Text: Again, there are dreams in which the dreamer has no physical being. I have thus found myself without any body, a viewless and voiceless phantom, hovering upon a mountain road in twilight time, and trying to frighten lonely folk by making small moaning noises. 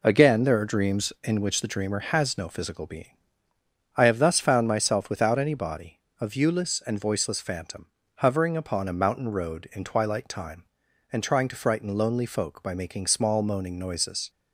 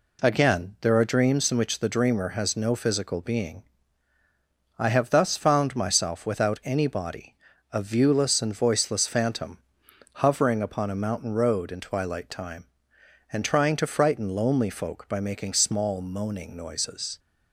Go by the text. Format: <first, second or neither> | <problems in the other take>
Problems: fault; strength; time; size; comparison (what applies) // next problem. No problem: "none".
neither | none